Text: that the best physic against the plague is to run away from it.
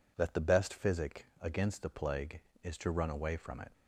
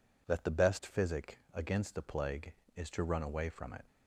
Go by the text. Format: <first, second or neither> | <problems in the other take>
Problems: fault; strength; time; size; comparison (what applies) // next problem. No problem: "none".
neither | pauses between "physic" and "against"; slight; the same in both